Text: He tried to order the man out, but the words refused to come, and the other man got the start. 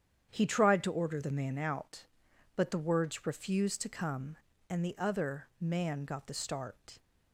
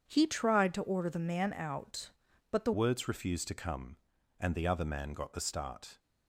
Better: first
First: starts louder than the rest; strong; until 1.3 s; 8.5 dB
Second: starts louder than the rest; strong; until 1.1 s; 7.5 dB // changes voice at "words"; from 2.7 s on; 3.2 s long

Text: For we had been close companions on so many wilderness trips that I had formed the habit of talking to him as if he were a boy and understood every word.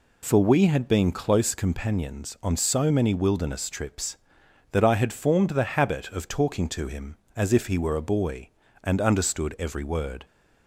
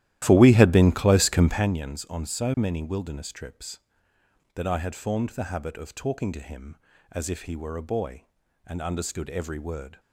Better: first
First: none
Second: starts louder than the rest; strong; until 1.8 s; 13.5 dB

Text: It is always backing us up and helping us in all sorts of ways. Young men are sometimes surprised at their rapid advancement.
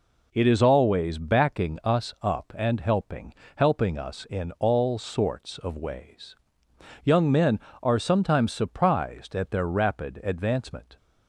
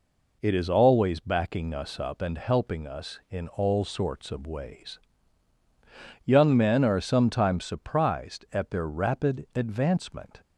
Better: second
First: says "helping" twice; at 3.5 s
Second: none

